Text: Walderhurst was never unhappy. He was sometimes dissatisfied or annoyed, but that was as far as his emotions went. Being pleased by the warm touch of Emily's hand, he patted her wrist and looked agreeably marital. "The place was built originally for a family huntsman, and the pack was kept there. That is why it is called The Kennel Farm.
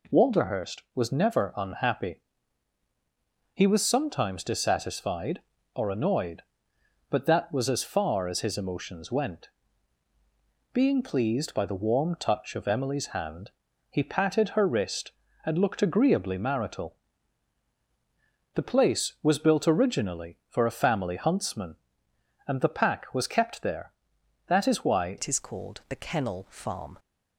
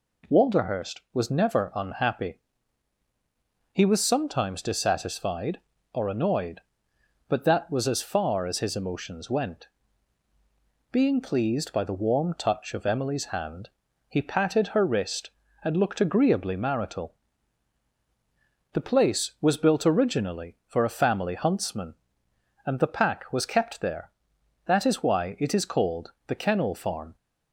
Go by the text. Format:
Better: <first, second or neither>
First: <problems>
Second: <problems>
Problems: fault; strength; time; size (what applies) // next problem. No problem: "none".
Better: second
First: changes voice at "it"; from 25.1 s on; 1.8 s long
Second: none